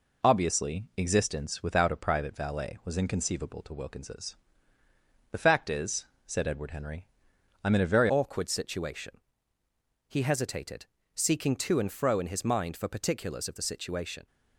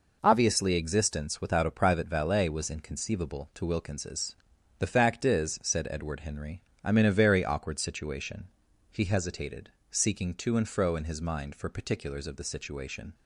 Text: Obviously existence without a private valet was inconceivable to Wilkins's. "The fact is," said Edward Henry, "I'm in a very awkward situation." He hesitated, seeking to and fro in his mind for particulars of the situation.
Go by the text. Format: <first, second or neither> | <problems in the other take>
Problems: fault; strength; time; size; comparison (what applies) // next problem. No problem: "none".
second | changes voice at "awkward"; from 8.0 s on; 6.2 s long